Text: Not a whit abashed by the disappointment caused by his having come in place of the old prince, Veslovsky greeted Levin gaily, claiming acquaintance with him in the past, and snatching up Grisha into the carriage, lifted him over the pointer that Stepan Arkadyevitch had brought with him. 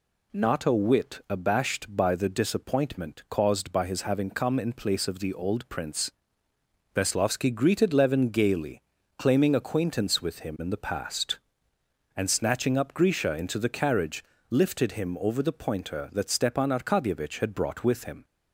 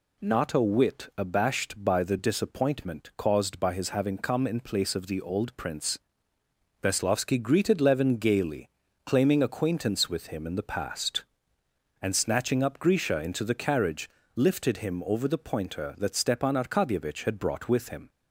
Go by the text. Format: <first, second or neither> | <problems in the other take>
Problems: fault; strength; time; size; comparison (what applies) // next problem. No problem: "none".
neither | none